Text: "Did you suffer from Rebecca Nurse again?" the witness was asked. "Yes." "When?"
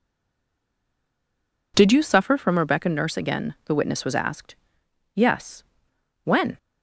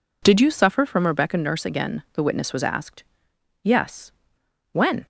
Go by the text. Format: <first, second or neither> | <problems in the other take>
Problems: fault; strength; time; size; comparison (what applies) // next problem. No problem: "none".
second | stays silent before the first word; noticeable; until 1.7 s; 1.7 s long